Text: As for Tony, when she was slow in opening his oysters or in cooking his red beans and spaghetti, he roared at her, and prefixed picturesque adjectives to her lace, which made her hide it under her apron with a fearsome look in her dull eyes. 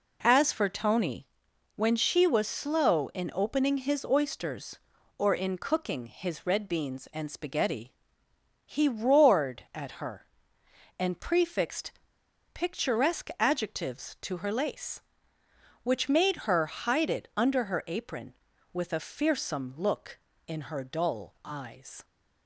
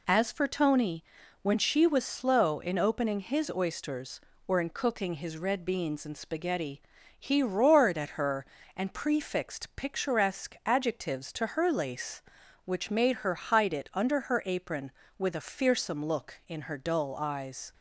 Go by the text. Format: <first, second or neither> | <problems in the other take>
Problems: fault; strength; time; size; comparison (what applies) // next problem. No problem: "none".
second | pauses between "prefixed" and "picturesque"; noticeable; at 11.9 s; 0.62 s long